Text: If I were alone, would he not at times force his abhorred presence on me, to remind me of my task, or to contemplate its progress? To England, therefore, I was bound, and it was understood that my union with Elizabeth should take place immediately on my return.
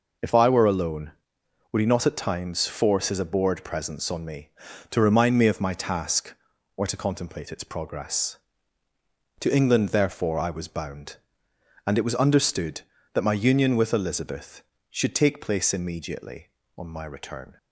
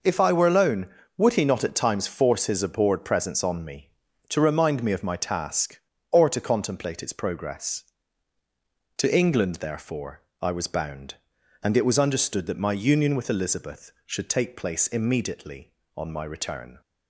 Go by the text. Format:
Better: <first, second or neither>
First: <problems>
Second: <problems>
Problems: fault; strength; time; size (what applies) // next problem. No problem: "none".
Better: neither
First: none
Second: none